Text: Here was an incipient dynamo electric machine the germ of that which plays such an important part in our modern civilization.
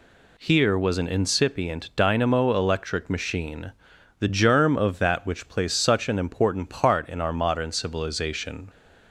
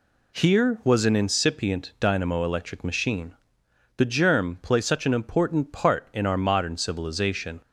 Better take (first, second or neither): first